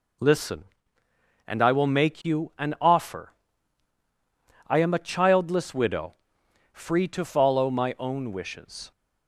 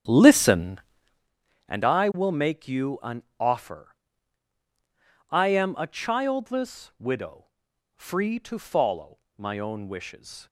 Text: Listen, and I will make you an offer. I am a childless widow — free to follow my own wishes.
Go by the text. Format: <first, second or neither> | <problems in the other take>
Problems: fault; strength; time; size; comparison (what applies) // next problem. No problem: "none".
first | starts louder than the rest; strong; until 1.3 s; 9.5 dB // pauses between "follow" and "my"; slight; at 9.1 s; 0.20 s long